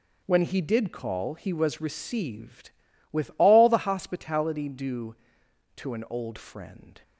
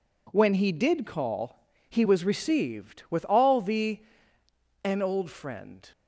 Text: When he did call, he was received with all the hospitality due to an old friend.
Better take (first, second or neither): first